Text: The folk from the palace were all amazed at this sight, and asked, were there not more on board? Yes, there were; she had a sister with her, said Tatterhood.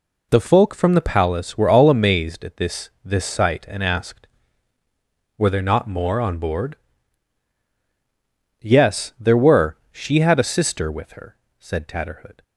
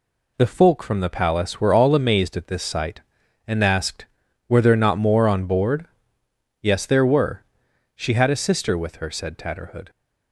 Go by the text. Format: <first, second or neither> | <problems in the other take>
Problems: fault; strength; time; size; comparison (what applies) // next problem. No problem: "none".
second | says "this" twice; at 3.0 s